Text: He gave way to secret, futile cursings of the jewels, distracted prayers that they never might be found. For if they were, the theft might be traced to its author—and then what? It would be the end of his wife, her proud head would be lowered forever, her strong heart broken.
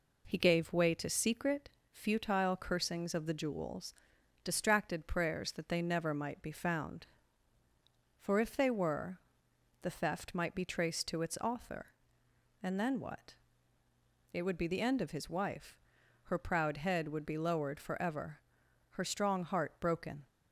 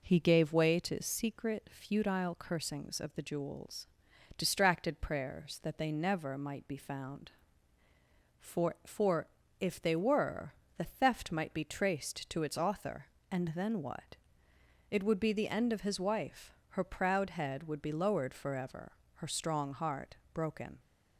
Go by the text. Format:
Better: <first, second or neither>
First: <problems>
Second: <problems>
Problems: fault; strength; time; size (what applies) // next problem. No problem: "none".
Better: first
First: none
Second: says "For" twice; at 8.8 s // pauses between "heart" and "broken"; slight; at 20.1 s; 0.16 s long